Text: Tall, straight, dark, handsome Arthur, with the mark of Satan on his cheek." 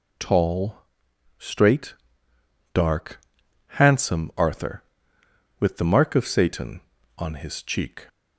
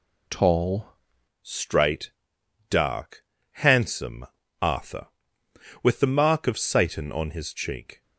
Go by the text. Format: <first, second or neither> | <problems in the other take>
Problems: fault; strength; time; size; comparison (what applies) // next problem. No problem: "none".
first | changes voice at "straight"; from 1.4 s on; 6.6 s long // pauses between "handsome" and "Arthur"; slight; at 4.2 s; 0.34 s long